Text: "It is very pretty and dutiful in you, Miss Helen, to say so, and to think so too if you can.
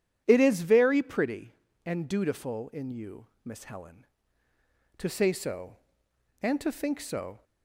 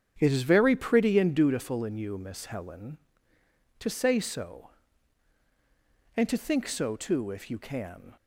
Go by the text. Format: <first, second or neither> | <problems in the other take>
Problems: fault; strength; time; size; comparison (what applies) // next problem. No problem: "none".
second | starts louder than the rest; strong; until 1.2 s; 9.5 dB; strong in the second // stops before "too if you can"; at 7.4 s